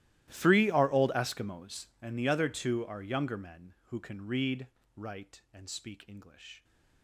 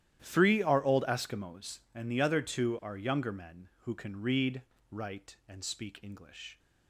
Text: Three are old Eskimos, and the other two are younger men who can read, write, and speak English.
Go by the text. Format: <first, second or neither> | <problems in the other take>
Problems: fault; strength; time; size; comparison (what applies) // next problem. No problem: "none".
second | gets quieter; strong; throughout; 23.5 dB // starts louder than the rest; strong; until 1.3 s; 15 dB; strong in the second